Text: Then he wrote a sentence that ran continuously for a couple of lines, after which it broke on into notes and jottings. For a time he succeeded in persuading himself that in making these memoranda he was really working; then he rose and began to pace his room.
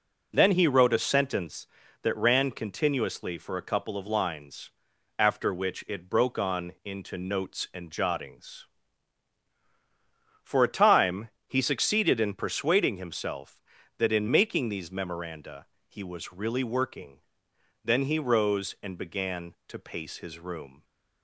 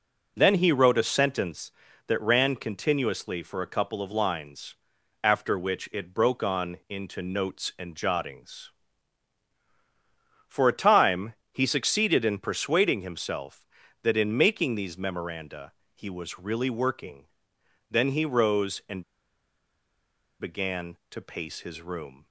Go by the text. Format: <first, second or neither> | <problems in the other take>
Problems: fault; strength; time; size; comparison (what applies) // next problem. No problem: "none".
first | pauses between "time" and "he"; slight; at 11.3 s; 0.18 s long; slight in the first // pauses between "memoranda" and "he"; slight; at 15.7 s; 0.22 s long; slight in the first // pauses between "and" and "began"; strong; at 19.0 s; 1.3 s long